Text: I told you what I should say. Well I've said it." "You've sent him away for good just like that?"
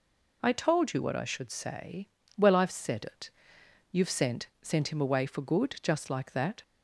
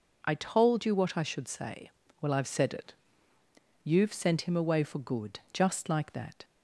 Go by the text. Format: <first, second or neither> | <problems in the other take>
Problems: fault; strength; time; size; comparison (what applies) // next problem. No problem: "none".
second | says "sent" twice; at 4.6 s